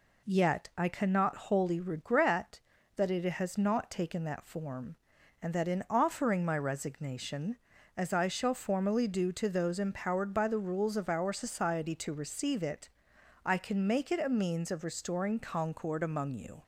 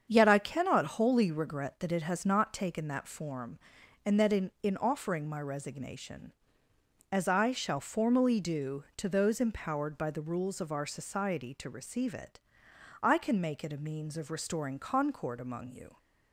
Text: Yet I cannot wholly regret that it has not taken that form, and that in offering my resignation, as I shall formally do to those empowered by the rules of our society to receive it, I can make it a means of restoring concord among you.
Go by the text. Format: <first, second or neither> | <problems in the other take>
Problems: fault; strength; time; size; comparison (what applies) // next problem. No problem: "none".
first | starts louder than the rest; strong; until 1.1 s; 7.5 dB // says "in" twice; at 4.6 s